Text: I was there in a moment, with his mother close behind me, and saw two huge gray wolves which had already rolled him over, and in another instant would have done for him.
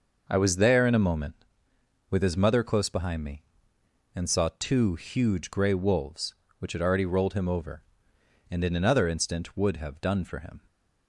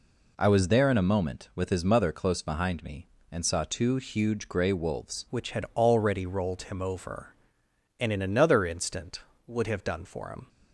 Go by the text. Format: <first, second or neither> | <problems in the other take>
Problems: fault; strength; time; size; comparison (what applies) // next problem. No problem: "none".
first | changes voice at "which"; from 5.2 s on; 5.2 s long